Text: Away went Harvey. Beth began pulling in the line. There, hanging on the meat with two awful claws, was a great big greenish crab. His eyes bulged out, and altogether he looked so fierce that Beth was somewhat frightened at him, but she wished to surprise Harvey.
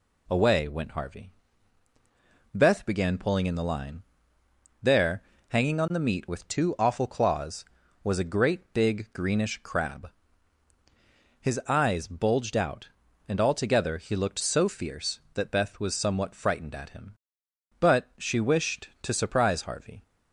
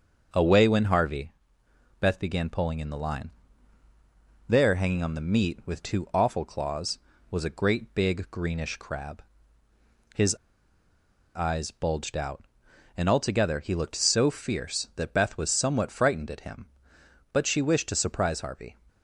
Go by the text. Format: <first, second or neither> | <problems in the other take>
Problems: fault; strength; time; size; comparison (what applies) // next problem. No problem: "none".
first | starts louder than the rest; until 1.3 s; 6.5 dB // pauses between "His" and "eyes"; at 10.3 s; 0.99 s long